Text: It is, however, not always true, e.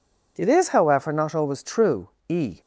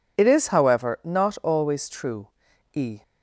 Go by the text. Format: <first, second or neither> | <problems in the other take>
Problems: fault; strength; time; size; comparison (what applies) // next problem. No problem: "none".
neither | none